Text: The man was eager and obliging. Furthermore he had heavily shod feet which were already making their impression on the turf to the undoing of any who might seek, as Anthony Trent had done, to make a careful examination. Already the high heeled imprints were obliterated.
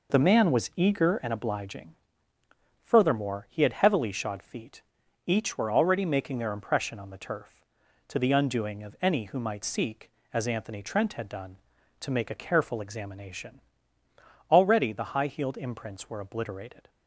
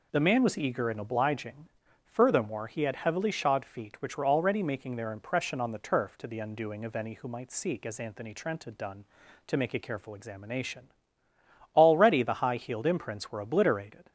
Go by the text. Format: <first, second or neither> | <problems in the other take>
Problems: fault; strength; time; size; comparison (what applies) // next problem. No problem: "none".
second | says "each" for "which"; at 5.2 s